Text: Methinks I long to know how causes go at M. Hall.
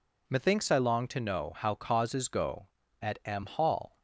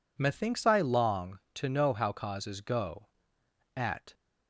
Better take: first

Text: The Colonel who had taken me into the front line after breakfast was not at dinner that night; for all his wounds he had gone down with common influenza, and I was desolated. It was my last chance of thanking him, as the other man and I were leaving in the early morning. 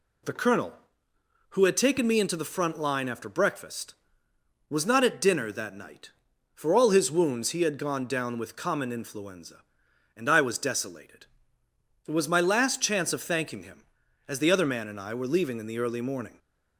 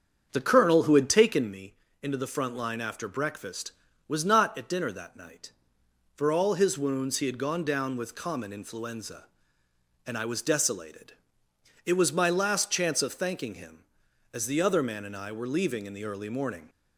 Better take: first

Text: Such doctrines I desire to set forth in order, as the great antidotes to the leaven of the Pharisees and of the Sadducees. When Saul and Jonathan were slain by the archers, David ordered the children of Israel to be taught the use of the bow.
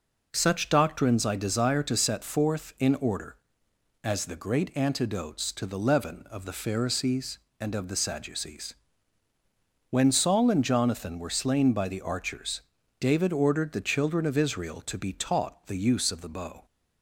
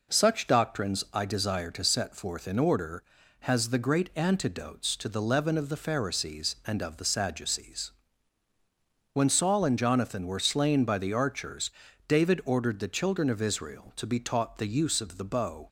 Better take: first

